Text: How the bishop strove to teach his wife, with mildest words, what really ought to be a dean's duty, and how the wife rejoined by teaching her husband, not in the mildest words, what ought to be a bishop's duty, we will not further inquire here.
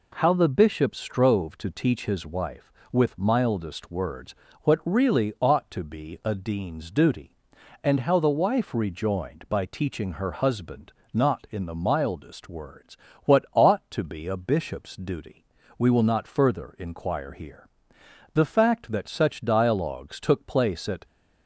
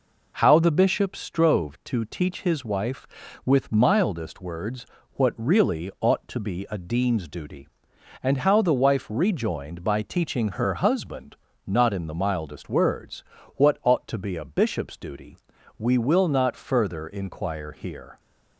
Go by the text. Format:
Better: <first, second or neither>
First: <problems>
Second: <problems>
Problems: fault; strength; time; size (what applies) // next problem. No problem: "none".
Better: second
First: goes on to say "The fact that such dialogues took place at"; strong; from 18.3 s on; 2.7 s long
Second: none